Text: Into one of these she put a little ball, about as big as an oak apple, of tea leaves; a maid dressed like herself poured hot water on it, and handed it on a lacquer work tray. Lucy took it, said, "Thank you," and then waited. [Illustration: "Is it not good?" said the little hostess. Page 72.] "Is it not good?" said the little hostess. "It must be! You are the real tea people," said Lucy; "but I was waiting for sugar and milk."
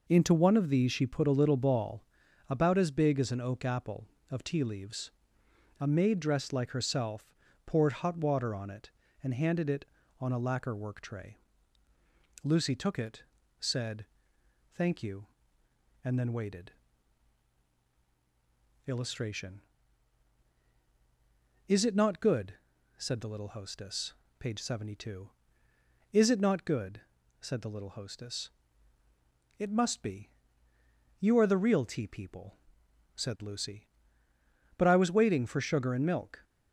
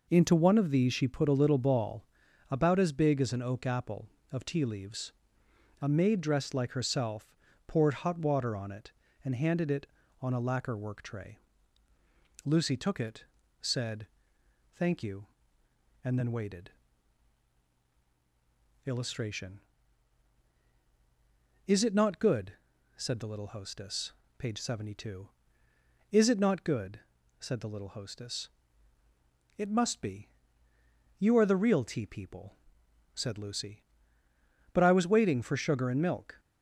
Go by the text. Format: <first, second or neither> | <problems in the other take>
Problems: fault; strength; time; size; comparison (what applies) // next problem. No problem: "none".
neither | pauses between "herself" and "poured"; slight; the same in both